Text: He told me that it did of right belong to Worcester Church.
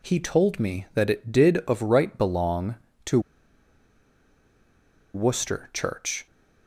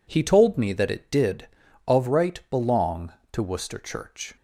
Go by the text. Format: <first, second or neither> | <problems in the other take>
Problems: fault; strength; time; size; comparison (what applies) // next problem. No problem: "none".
second | pauses between "to" and "Worcester"; strong; at 3.1 s; 1.9 s long